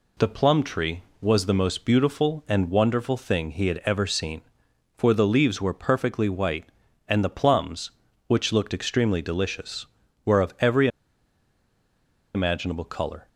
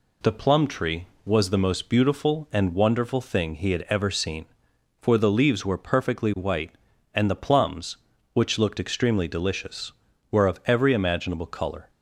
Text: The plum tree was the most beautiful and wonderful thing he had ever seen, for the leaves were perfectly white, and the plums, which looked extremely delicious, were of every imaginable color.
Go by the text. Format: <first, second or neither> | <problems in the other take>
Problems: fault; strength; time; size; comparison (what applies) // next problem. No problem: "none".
second | pauses between "every" and "imaginable"; strong; at 10.8 s; 1.4 s long